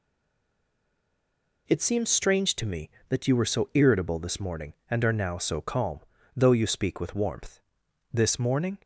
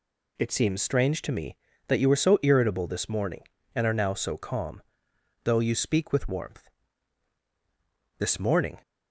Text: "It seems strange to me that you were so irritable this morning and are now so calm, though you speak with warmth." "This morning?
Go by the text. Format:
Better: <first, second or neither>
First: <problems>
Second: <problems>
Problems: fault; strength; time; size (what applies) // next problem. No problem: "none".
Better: second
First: stays silent before the first word; noticeable; until 1.6 s; 1.6 s long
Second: none